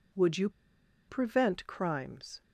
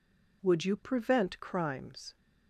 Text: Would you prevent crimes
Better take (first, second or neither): second